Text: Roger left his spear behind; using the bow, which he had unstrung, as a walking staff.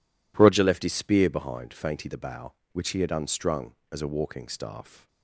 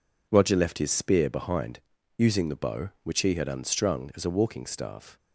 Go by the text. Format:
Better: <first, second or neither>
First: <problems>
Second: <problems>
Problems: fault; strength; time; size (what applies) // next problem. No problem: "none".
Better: second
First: says "fainty" for "using"; at 1.7 s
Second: none